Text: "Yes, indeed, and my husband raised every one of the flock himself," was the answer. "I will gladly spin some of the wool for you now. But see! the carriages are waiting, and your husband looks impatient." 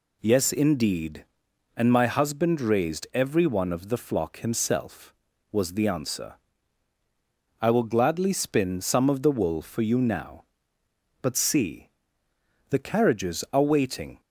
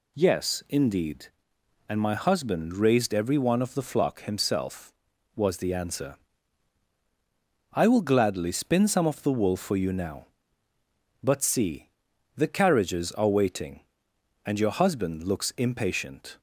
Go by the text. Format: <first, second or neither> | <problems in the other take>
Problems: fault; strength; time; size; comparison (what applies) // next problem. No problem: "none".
second | stops before "and your husband looks impatient"; at 14.2 s